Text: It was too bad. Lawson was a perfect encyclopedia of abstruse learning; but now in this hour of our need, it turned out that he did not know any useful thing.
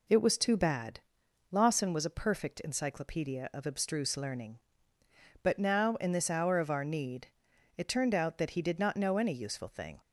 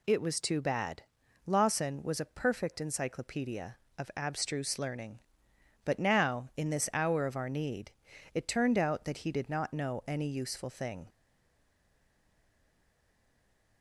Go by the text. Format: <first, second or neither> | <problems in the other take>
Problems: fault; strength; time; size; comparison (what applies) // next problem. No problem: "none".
first | stays silent after the last word; strong; from 11.0 s on; 2.8 s long